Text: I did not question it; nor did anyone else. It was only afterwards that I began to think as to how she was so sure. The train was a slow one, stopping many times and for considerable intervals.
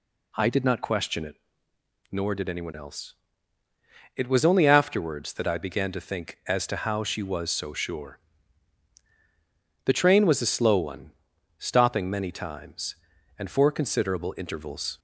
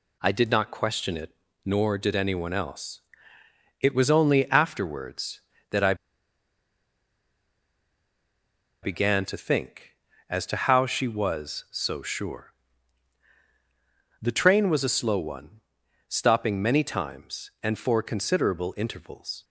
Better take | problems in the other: first | pauses between "I" and "began"; strong; at 5.9 s; 2.8 s long

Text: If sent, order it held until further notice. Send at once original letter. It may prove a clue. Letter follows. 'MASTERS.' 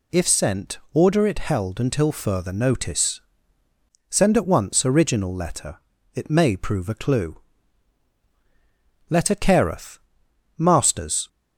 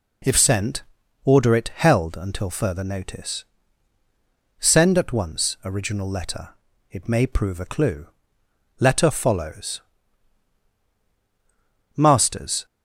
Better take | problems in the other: second | says "careth" for "follows"; at 9.3 s

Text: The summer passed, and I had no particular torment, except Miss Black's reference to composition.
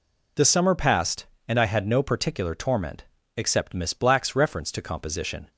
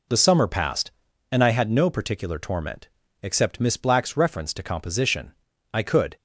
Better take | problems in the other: first | goes on to say "I could"; slight; from 5.7 s on; 0.42 s long

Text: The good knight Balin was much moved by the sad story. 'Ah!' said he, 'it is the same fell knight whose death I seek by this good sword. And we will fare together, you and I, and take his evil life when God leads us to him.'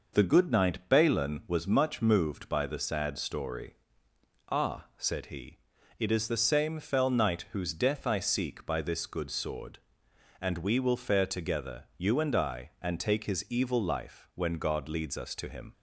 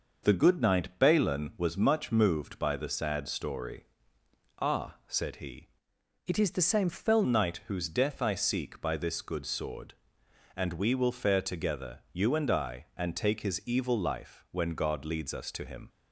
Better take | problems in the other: first | changes voice from "it" to "fell"; from 6.2 to 7.2 s; 1.0 s long

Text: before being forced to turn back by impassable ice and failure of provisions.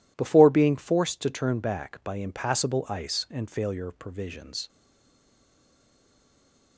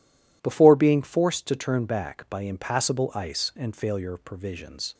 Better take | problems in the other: second | stays silent after the last word; noticeable; from 4.6 s on; 2.1 s long

